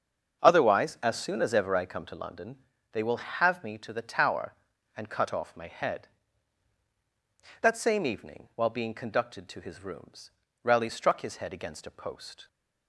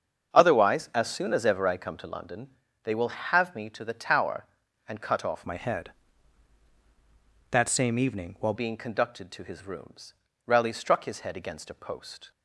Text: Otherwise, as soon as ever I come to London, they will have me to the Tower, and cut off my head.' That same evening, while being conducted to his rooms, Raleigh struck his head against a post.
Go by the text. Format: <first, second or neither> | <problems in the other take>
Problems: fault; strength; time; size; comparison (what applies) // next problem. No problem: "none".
first | starts louder than the rest; until 1.3 s; 7 dB; also in the first // changes voice from "my" to "while"; from 5.4 to 8.5 s; 3.1 s long